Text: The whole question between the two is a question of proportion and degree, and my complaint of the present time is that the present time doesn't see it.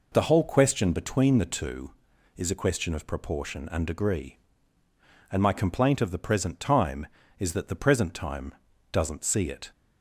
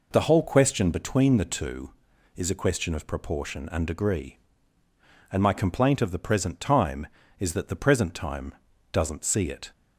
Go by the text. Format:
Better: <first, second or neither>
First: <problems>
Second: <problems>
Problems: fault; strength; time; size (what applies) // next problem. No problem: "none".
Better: neither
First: pauses between "time" and "doesn't"; at 8.5 s; 0.38 s long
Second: pauses between "time" and "doesn't"; at 8.5 s; 0.38 s long